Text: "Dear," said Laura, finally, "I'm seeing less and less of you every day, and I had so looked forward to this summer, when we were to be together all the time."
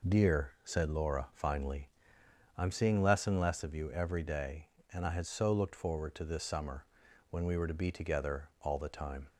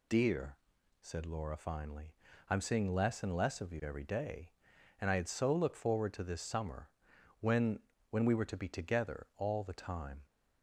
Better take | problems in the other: first | says "when" twice; at 8.0 s

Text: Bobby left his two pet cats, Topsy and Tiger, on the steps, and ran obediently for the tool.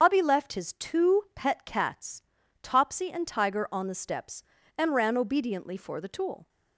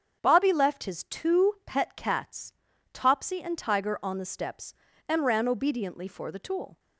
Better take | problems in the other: second | loses the start of "Bobby"; at 0.0 s; 105 ms // starts louder than the rest; until 1.0 s; 7 dB; strong in the second

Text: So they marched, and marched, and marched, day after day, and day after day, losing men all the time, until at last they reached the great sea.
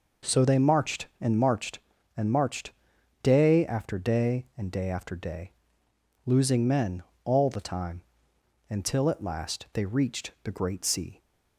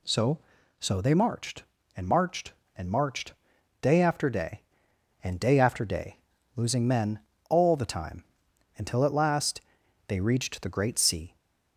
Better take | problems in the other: first | says "So" twice; at 0.7 s // pauses between "men" and "all"; slight; at 7.2 s; 0.28 s long; slight in the first // pauses between "last" and "they"; noticeable; at 9.6 s; 0.46 s long

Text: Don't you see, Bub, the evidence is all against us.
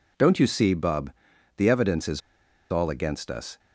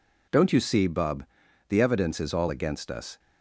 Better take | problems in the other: second | pauses between "is" and "all"; noticeable; at 2.2 s; 0.52 s long

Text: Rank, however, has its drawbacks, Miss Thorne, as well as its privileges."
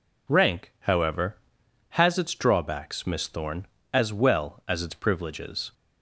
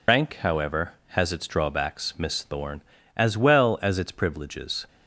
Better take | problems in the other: first | loses the start of "Rank"; at 0.0 s; 70 ms

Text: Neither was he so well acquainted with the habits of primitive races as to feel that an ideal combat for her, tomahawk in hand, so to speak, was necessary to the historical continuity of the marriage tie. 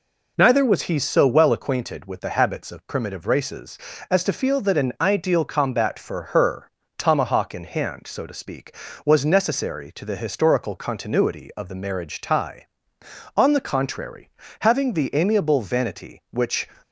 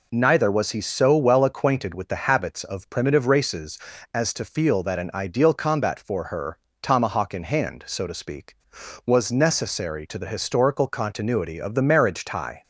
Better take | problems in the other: second | goes on to say "On the contrary having the amiable vanity which"; strong; from 13.3 s on; 3.3 s long

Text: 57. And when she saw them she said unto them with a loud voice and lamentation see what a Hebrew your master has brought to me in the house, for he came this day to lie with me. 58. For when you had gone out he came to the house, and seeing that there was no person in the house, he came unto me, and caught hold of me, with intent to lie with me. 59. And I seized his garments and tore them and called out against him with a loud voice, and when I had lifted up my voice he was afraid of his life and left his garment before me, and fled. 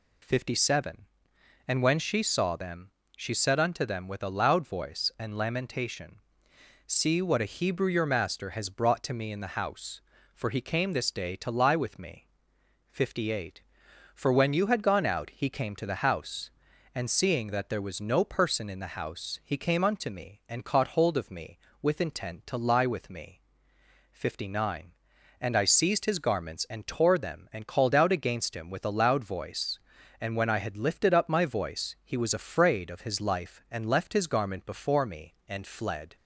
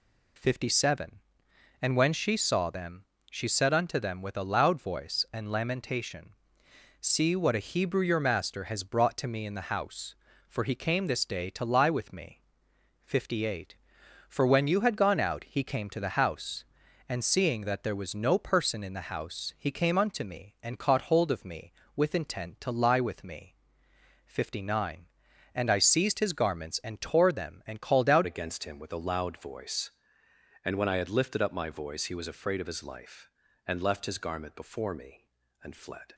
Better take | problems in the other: first | pauses between "them" and "she"; slight; at 3.0 s; 0.26 s long; slight in the first // pauses between "lamentation" and "see"; noticeable; at 6.3 s; 0.66 s long; noticeable in the first // changes voice at "against"; from 28.2 s on; 7.9 s long

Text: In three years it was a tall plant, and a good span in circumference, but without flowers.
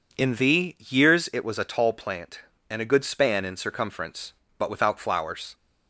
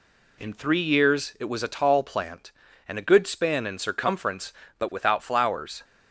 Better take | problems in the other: second | says "thee" for "three"; at 0.3 s

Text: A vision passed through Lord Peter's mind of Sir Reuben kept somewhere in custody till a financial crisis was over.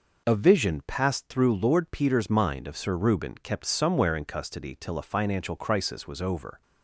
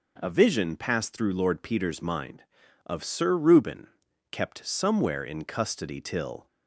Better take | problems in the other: first | pauses between "Reuben" and "kept"; at 3.8 s; 0.44 s long // stops before "a financial crisis was over"; at 6.4 s

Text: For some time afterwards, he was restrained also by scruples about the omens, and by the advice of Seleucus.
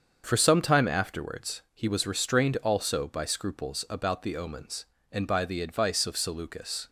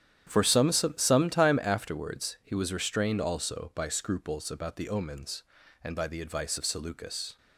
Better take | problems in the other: first | starts louder than the rest; strong; until 1.2 s; 9.5 dB; also in the first // says "some" twice; at 0.7 s

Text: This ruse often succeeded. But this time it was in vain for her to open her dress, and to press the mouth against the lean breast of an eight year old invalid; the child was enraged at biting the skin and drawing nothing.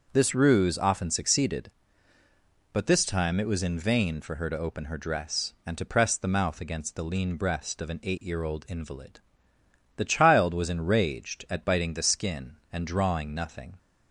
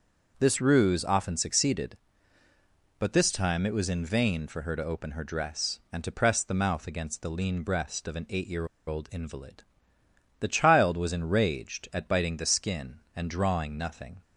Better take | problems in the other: first | pauses between "year" and "old"; slight; at 8.6 s; 0.19 s long

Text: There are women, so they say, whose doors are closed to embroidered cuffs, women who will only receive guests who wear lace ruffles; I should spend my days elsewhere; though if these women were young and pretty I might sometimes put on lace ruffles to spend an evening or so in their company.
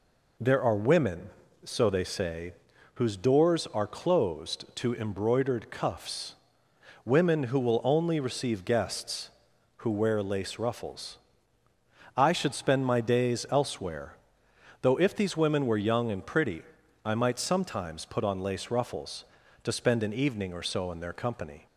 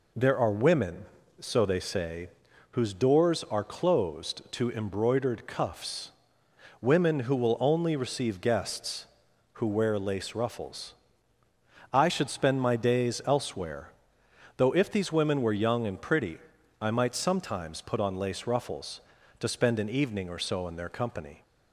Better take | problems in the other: neither | pauses between "pretty" and "I"; the same in both

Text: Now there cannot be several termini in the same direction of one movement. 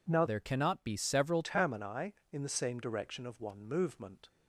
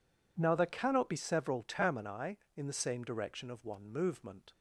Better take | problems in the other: second | changes voice from "there" to "several"; from 0.2 to 1.4 s; 1.2 s long

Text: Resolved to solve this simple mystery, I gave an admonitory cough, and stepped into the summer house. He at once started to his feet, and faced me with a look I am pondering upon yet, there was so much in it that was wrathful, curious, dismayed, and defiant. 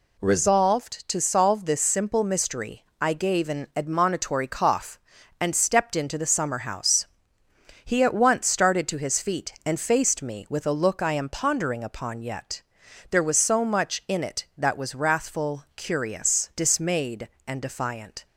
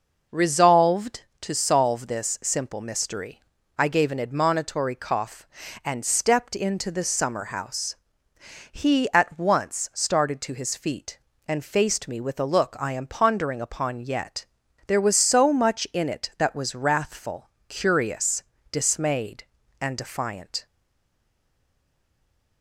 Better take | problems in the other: first | stays silent after the last word; noticeable; from 20.6 s on; 2.0 s long

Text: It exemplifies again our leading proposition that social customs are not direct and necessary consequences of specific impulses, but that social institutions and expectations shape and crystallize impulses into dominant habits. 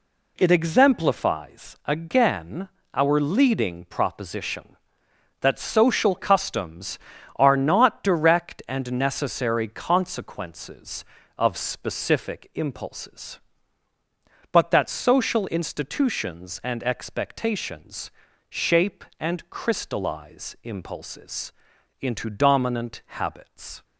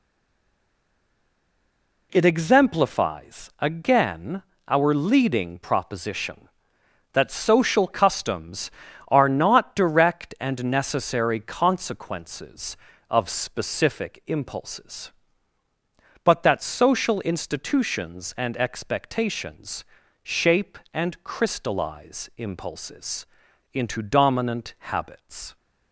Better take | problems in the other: first | stays silent before the first word; until 2.1 s; 2.1 s long // pauses between "again" and "our"; slight; at 4.4 s; 0.24 s long; slight in the first // pauses between "expectations" and "shape"; at 19.8 s; 0.38 s long; also in the first // pauses between "impulses" and "into"; noticeable; at 23.2 s; 0.46 s long; noticeable in the first

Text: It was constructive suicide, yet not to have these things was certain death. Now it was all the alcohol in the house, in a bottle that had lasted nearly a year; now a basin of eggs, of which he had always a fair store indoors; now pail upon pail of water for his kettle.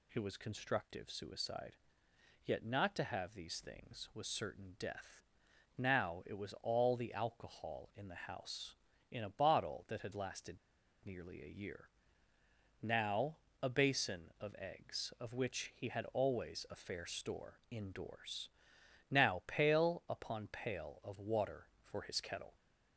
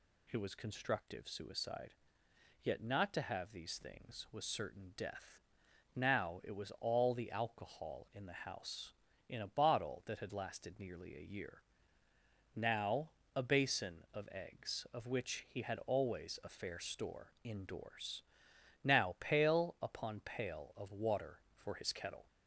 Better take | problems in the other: second | pauses between "lasted" and "nearly"; noticeable; at 10.5 s; 0.48 s long // pauses between "now" and "a"; slight; at 13.3 s; 0.26 s long; slight in the second

